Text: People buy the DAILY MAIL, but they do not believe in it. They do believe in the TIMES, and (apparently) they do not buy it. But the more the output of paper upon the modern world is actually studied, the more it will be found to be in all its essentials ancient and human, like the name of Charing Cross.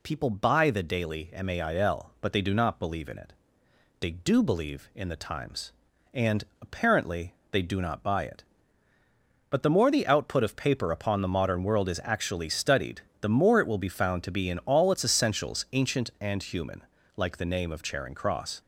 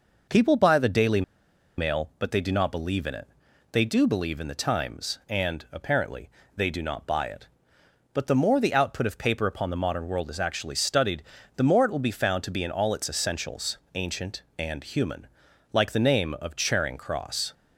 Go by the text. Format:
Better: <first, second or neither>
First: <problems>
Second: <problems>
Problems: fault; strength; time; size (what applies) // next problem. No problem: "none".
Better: first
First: none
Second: pauses between "DAILY" and "MAIL"; noticeable; at 1.2 s; 0.56 s long // pauses between "essentials" and "ancient"; slight; at 13.7 s; 0.16 s long